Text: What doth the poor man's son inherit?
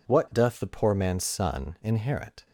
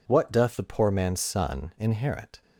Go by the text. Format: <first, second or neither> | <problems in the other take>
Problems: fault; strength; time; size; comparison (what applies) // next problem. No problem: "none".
neither | none